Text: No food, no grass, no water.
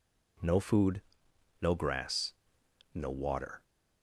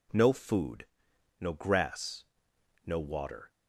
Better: neither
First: none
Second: none

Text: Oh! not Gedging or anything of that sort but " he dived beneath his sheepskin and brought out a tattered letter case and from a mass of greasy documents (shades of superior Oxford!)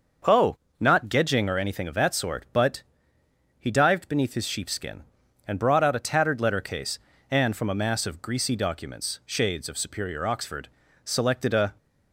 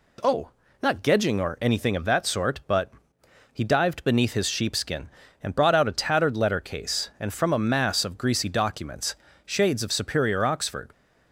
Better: second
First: starts louder than the rest; until 1.4 s; 6 dB // goes on to say "selected a"; noticeable; from 11.0 s on; 0.72 s long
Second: none

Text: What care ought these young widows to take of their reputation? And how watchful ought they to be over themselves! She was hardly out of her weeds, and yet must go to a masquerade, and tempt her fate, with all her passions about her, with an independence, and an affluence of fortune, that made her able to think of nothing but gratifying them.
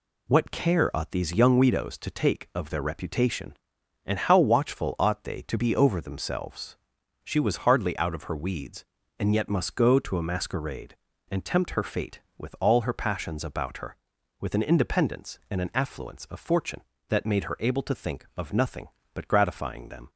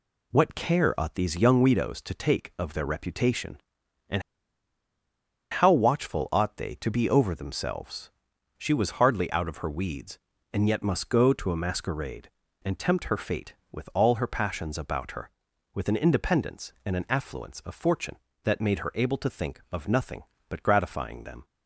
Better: first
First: none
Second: pauses between "And" and "how"; strong; at 4.2 s; 1.2 s long

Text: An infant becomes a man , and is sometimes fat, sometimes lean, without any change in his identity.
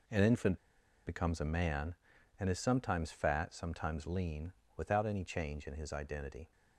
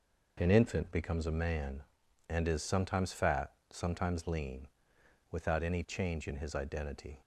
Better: second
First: pauses between "infant" and "becomes"; noticeable; at 0.5 s; 0.49 s long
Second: none

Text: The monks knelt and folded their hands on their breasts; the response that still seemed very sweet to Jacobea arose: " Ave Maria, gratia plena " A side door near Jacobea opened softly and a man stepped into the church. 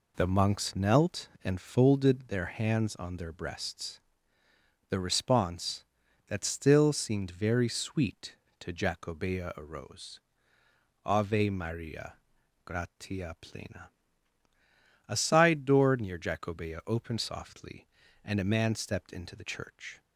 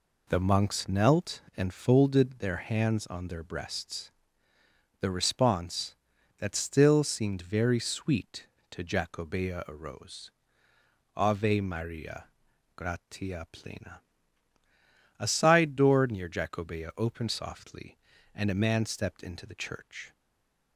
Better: first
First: none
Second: stays silent after the last word; slight; from 20.1 s on; 0.6 s long

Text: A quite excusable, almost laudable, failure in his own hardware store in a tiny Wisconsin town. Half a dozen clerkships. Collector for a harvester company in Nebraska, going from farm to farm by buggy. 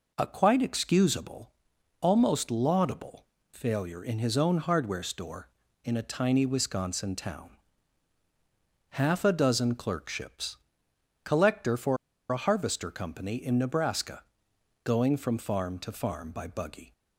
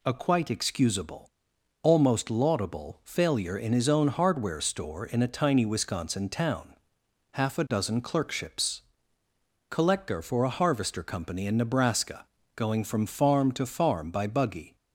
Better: second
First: pauses between "for" and "a"; slight; at 11.9 s; 0.33 s long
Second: none

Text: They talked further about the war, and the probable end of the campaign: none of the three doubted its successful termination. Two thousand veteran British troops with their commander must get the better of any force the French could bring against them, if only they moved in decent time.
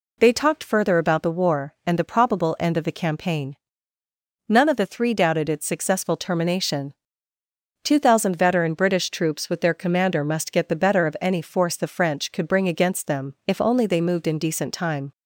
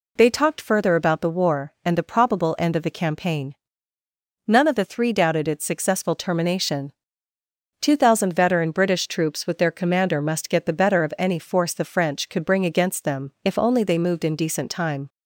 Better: neither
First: none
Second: none

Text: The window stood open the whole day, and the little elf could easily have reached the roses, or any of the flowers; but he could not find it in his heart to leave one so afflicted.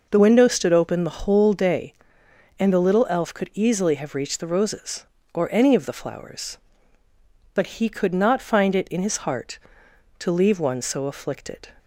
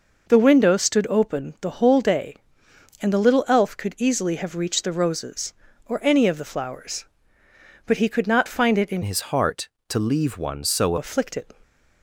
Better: first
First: none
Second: changes voice from "his" to "so"; from 9.0 to 10.9 s; 1.9 s long

